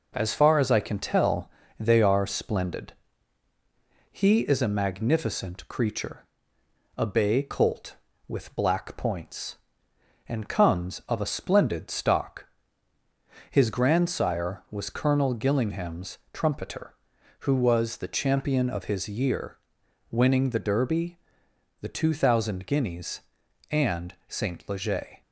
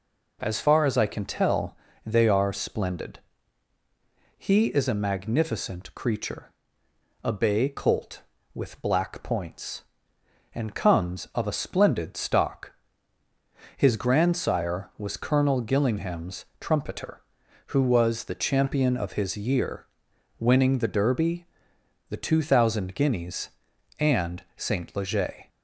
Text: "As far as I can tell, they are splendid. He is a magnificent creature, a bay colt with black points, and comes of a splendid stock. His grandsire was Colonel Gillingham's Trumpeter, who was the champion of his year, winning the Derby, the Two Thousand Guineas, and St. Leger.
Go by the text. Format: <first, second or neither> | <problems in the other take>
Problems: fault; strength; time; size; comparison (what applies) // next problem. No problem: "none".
second | gets quieter; slight; throughout; 3 dB